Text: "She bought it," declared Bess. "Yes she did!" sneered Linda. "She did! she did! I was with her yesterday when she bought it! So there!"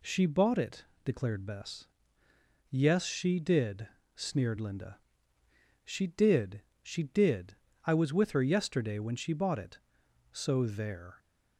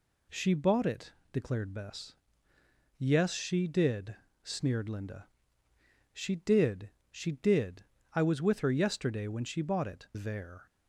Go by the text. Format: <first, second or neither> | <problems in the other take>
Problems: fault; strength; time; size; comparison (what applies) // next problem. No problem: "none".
first | skips "So"; at 10.1 s